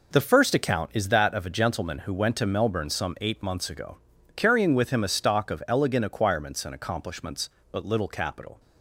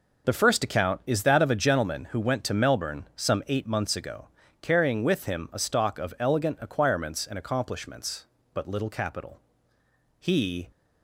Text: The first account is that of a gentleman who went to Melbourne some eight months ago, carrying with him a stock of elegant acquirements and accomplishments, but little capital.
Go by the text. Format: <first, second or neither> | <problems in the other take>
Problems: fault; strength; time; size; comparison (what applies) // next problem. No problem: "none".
first | goes on to say "He"; from 10.1 s on; 0.52 s long